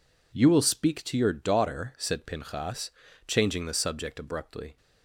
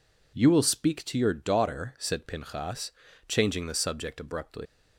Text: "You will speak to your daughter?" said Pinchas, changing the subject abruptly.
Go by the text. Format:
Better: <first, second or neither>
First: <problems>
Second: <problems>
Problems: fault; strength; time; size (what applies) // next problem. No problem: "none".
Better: first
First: none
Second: leaves "abruptly" unfinished; at 4.6 s; 115 ms